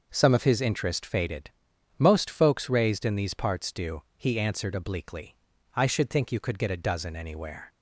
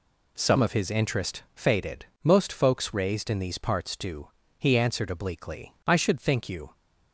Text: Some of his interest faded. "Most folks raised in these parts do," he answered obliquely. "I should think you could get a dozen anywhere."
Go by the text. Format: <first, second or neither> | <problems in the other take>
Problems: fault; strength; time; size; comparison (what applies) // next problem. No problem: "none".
first | stops before "could get a dozen anywhere"; at 6.7 s